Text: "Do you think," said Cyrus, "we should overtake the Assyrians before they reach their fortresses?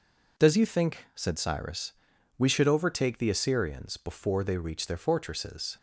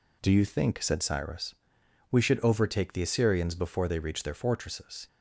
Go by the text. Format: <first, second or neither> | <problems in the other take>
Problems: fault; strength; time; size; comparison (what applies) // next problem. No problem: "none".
second | says "Does" for "Do"; at 0.3 s